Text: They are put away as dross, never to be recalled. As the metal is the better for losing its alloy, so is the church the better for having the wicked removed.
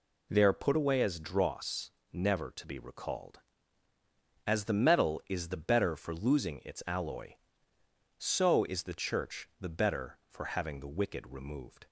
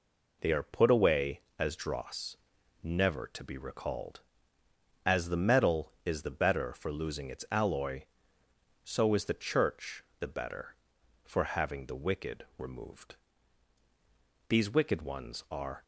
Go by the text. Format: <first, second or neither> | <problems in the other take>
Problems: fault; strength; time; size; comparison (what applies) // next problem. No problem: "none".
first | pauses between "church" and "the"; slight; at 10.0 s; 0.16 s long // goes on to say "These wicked ones are"; from 14.4 s on; 1.3 s long